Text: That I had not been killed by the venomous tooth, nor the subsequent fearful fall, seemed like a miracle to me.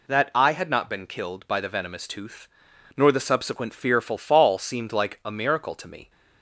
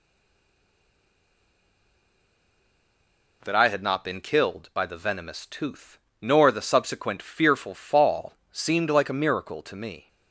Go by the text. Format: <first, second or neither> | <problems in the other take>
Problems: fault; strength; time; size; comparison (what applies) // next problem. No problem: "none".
first | stays silent before the first word; strong; until 3.4 s; 3.4 s long